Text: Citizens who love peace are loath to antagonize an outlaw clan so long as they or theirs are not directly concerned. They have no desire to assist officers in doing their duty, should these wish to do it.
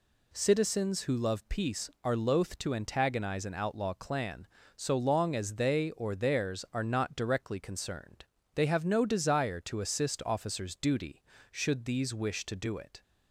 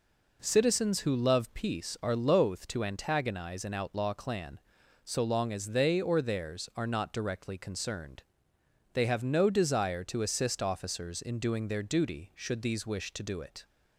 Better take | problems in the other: second | skips "in doing their"; at 10.7 s

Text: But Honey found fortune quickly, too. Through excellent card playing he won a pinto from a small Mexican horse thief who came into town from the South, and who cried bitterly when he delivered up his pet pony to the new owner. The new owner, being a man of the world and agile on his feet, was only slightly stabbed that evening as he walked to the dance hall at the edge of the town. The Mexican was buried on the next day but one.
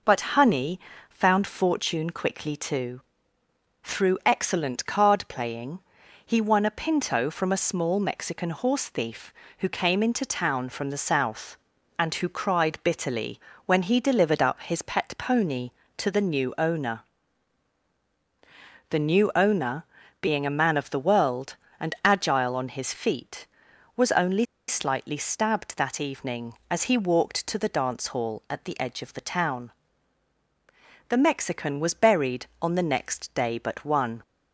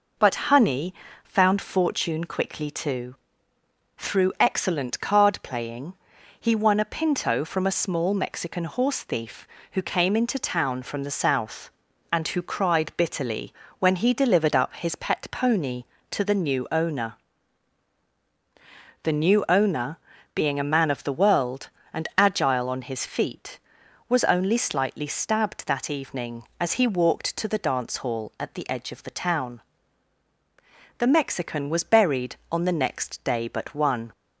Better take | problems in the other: second | pauses between "Honey" and "found"; slight; at 0.7 s; 0.30 s long; slight in the second // pauses between "playing" and "he"; noticeable; at 5.7 s; 0.46 s long; noticeable in the second // pauses between "bitterly" and "when"; slight; at 13.3 s; 0.26 s long; slight in the second // pauses between "only" and "slightly"; slight; at 24.4 s; 0.23 s long

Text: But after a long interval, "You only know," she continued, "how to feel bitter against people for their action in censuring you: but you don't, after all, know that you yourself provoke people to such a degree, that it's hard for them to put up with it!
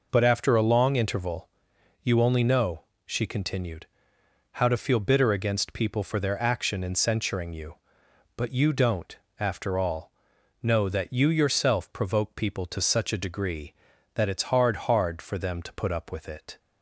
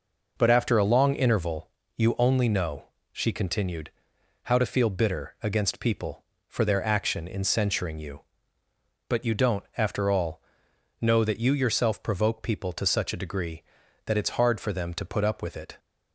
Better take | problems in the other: second | says "hard" twice; at 14.7 s

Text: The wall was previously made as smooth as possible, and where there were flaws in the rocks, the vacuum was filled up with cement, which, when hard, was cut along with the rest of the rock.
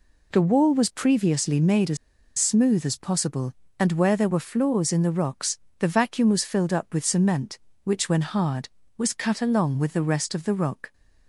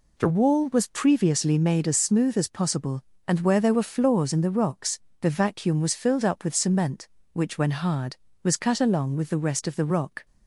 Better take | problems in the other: second | pauses between "as" and "smooth"; at 1.9 s; 0.41 s long

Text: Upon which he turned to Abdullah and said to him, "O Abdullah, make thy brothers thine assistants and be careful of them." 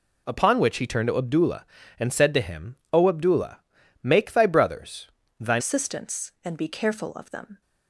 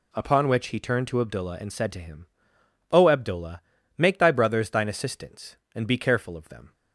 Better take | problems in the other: second | pauses between "brothers" and "thine"; slight; at 5.0 s; 0.32 s long // changes voice at "assistants"; from 5.5 s on; 2.1 s long

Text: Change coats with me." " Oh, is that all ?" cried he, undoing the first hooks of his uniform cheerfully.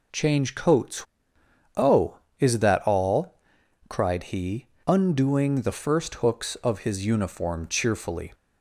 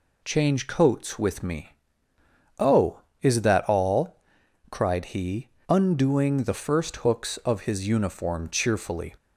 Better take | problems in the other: second | skips "with me"; at 1.1 s

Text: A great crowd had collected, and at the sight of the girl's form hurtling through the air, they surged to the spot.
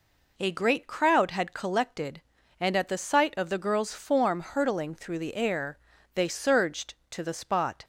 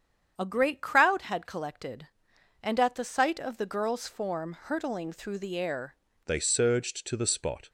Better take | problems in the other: first | starts louder than the rest; strong; until 1.3 s; 8 dB // changes voice at "they"; from 6.2 s on; 1.4 s long

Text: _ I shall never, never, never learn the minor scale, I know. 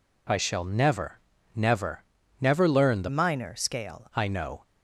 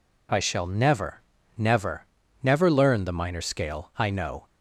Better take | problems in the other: second | changes voice from "minor" to "scale"; from 3.0 to 4.0 s; 1.0 s long

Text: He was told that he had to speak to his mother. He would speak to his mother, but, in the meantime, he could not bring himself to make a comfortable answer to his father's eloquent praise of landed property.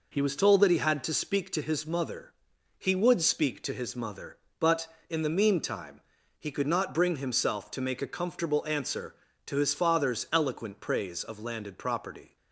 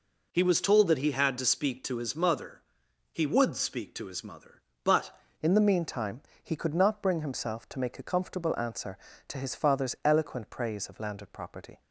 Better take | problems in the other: first | changes voice at "in"; from 5.4 s on; 6.4 s long

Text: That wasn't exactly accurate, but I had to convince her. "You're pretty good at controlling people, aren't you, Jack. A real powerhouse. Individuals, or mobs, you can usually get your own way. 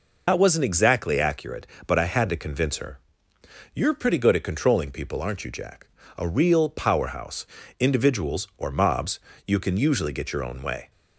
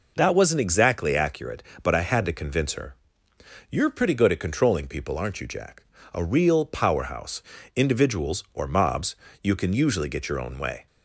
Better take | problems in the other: second | loses the start of "That"; at 0.2 s; 75 ms

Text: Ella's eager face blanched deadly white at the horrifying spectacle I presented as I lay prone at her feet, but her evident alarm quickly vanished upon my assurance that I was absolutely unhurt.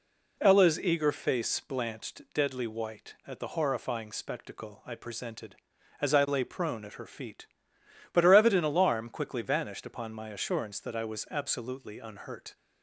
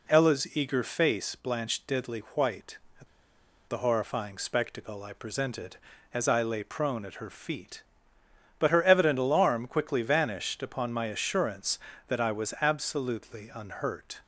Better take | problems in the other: first | pauses between "deadly" and "white"; slight; at 2.2 s; 0.16 s long // pauses between "at" and "the"; noticeable; at 3.0 s; 0.62 s long

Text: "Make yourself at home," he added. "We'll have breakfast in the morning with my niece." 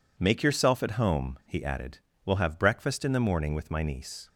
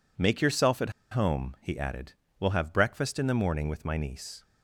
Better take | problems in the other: first | pauses between "at" and "home"; slight; at 0.8 s; 0.21 s long

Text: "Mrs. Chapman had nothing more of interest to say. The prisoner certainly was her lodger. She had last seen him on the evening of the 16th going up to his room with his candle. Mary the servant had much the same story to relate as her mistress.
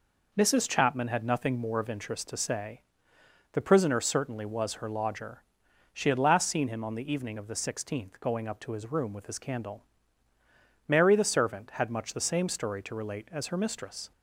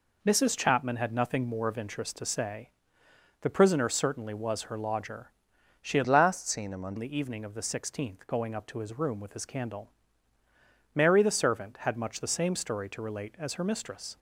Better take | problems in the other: first | changes voice from "last" to "on"; from 6.0 to 6.9 s; 0.9 s long

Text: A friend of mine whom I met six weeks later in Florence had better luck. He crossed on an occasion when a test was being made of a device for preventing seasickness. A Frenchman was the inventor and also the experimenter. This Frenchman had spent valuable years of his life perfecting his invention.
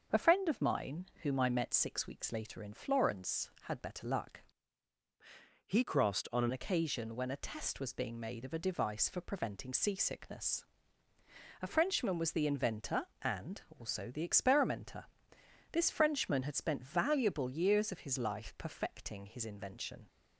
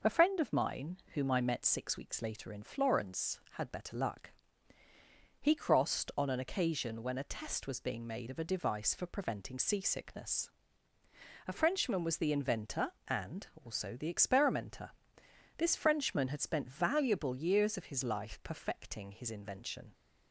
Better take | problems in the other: second | starts louder than the rest; until 1.3 s; 6.5 dB // pauses between "mine" and "whom"; slight; at 1.0 s; 0.18 s long; slight in the second // changes voice from "He" to "an"; from 5.6 to 6.5 s; 0.9 s long // pauses between "and" and "also"; slight; at 13.6 s; 0.18 s long; slight in the second

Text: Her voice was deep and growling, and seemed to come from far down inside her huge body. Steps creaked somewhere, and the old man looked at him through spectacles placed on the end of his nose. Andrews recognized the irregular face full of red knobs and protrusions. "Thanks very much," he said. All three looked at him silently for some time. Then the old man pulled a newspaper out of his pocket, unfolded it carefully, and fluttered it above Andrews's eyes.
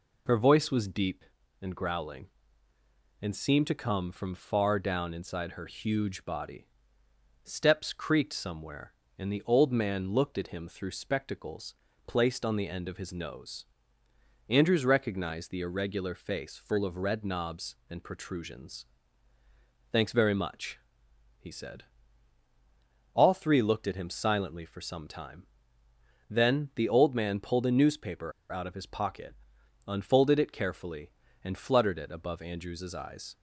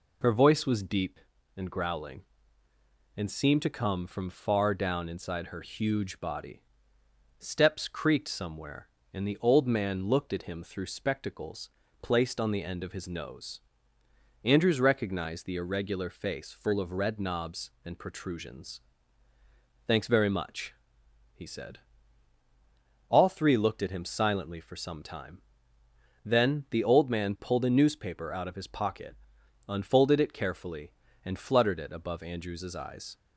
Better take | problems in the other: second | pauses between "spectacles" and "placed"; slight; at 11.7 s; 0.32 s long; slight in the second // pauses between "newspaper" and "out"; slight; at 28.3 s; 0.20 s long

